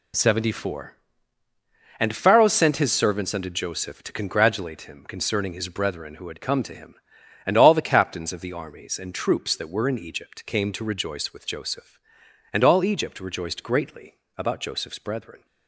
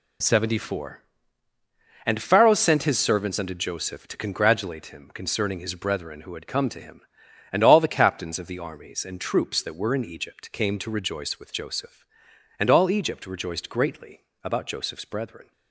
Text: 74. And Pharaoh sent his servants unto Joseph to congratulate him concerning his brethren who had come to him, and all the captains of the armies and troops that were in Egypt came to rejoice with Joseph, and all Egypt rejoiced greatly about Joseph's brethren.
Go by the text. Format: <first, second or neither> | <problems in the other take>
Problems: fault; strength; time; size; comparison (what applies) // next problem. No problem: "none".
neither | pauses between "greatly" and "about"; slight; the same in both